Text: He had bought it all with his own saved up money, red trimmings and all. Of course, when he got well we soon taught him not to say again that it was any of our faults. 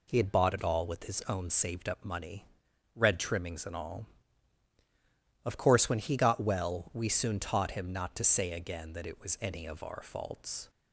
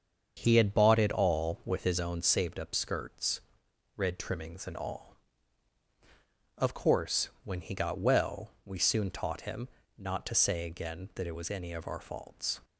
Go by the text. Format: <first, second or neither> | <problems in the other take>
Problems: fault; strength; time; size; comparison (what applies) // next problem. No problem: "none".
first | starts louder than the rest; until 1.4 s; 7 dB // says "skirts" for "money"; at 2.7 s // pauses between "well" and "we"; slight; at 8.5 s; 0.16 s long // pauses between "him" and "not"; slight; at 9.7 s; 0.26 s long